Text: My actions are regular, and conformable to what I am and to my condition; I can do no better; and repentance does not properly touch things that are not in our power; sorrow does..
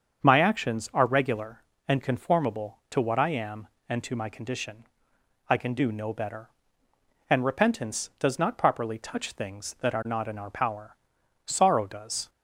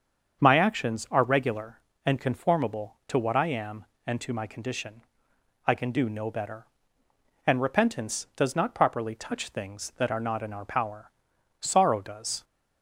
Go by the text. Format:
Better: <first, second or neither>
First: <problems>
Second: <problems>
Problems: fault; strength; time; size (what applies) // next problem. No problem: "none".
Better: neither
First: starts louder than the rest; until 1.2 s; 7 dB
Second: starts louder than the rest; until 1.4 s; 7 dB